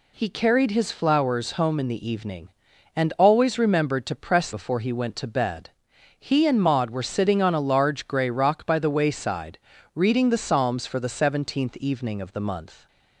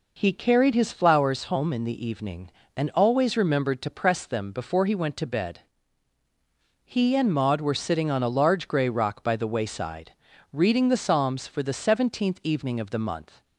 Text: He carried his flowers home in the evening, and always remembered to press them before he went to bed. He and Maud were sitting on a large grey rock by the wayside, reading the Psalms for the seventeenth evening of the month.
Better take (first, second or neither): second